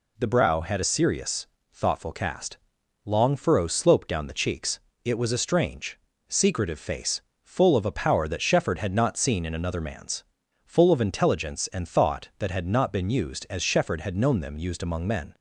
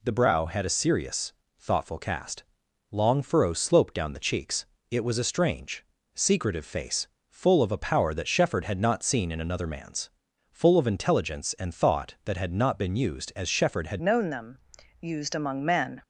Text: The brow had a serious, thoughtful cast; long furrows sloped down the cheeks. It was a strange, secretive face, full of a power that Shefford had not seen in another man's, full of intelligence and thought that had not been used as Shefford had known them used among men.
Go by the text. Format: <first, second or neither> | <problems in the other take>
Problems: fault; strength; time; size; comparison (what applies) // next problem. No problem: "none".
first | changes voice at "known"; from 14.0 s on; 2.0 s long // pauses between "them" and "used"; at 14.5 s; 0.42 s long